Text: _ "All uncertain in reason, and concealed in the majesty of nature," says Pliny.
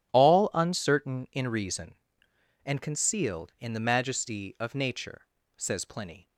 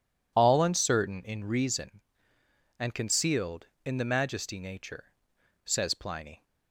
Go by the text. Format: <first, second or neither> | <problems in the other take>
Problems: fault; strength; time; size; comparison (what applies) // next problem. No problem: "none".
first | skips "of"; at 4.5 s